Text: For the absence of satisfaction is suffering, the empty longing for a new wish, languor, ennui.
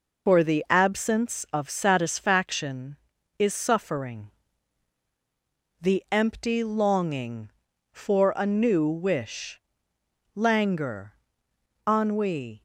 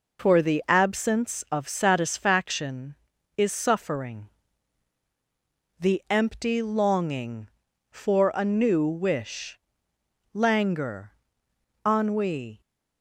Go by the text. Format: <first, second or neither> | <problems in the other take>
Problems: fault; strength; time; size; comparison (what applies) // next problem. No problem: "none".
second | loses the start of "For"; at 0.2 s; 50 ms